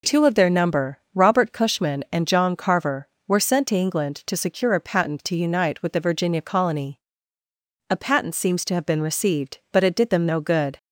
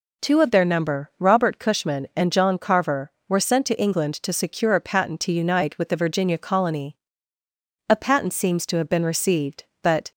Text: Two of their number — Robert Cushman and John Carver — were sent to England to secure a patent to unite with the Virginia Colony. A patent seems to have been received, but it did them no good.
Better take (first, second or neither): first